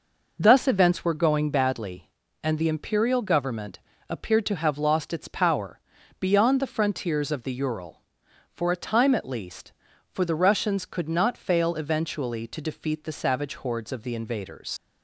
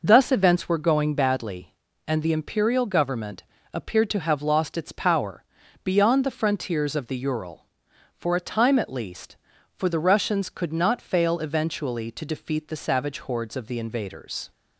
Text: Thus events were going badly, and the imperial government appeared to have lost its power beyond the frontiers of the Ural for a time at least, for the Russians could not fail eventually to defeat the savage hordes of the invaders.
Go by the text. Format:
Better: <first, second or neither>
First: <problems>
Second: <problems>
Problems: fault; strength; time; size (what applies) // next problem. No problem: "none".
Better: second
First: pauses between "government" and "appeared"; slight; at 3.8 s; 0.28 s long // pauses between "power" and "beyond"; at 5.8 s; 0.40 s long // leaves "invaders" unfinished; at 14.7 s; 95 ms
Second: pauses between "government" and "appeared"; slight; at 3.4 s; 0.28 s long // pauses between "power" and "beyond"; at 5.4 s; 0.40 s long